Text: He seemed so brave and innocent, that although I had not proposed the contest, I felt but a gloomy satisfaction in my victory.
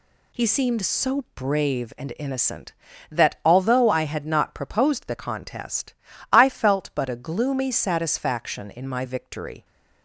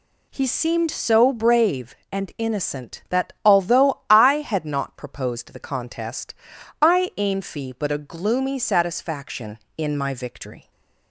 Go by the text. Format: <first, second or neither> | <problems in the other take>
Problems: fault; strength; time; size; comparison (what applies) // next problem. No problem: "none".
first | says "ainfi" for "felt"; at 7.1 s